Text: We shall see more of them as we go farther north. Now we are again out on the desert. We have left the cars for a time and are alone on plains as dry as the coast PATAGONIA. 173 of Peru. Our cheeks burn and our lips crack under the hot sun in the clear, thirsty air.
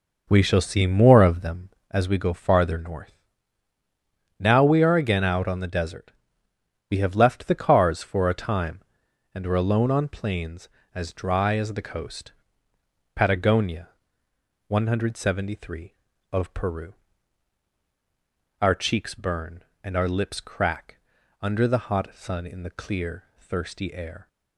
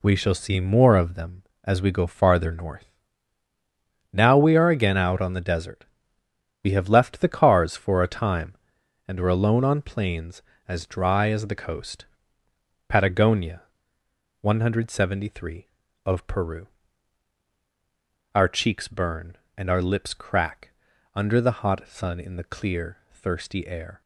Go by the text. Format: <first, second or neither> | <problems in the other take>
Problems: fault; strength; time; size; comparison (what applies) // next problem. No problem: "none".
second | starts louder than the rest; noticeable; until 2.1 s; 5.5 dB // pauses between "coast" and "PATAGONIA"; noticeable; at 12.3 s; 0.84 s long; noticeable in the second // pauses between "crack" and "under"; at 20.9 s; 0.44 s long; also in the second